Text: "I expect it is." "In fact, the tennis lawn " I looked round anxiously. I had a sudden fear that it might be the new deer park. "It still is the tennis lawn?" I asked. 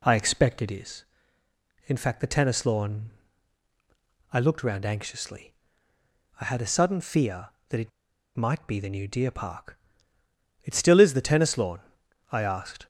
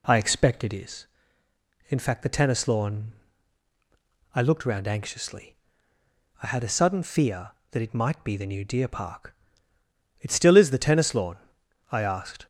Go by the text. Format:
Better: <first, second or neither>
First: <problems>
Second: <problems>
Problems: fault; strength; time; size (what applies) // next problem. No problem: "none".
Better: second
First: pauses between "it" and "might"; noticeable; at 7.9 s; 0.46 s long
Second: none